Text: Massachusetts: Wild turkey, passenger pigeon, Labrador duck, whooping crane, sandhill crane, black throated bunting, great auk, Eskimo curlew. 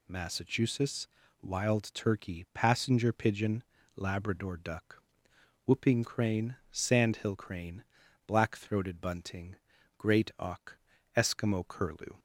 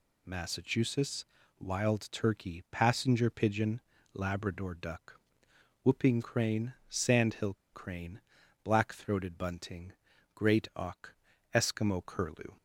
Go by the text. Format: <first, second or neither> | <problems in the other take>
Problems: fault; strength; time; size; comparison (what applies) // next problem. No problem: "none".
first | pauses between "sandhill" and "crane"; slight; at 7.5 s; 0.19 s long